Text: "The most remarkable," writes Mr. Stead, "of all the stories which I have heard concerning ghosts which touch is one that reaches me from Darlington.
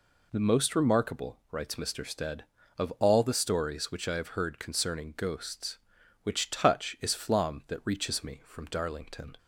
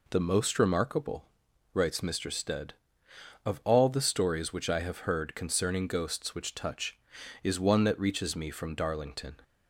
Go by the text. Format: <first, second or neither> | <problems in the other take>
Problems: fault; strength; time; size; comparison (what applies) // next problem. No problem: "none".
second | says "flom" for "one"; at 7.1 s